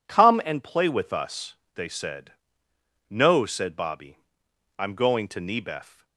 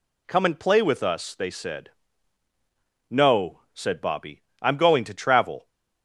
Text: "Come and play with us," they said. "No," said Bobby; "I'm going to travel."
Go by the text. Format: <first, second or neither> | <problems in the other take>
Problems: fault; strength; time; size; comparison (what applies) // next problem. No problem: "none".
second | says "nebef" for "travel"; at 5.4 s